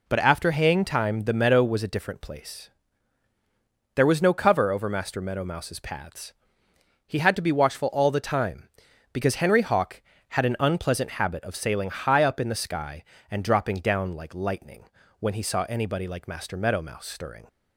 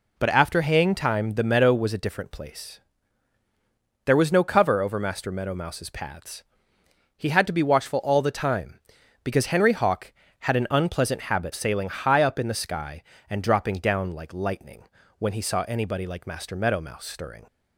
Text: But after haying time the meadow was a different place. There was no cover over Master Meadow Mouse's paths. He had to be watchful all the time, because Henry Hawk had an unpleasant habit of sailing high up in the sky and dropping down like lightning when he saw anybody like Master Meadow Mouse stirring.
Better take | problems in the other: first | skips "of"; at 11.5 s // pauses between "lightning" and "when"; slight; at 14.8 s; 0.36 s long; slight in the first

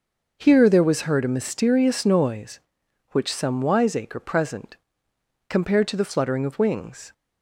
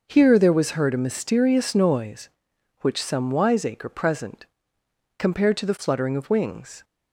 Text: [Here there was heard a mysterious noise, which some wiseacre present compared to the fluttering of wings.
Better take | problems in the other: neither | pauses between "present" and "compared"; noticeable; the same in both

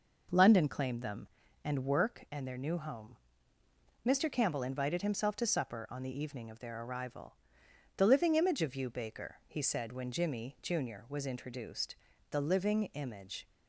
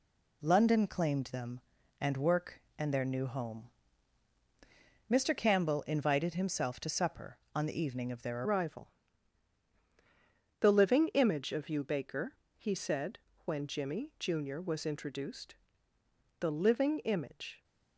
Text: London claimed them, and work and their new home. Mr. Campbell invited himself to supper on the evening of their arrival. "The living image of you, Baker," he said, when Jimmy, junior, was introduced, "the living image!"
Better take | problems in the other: first | changes voice at "arrival"; from 8.4 s on; 9.2 s long

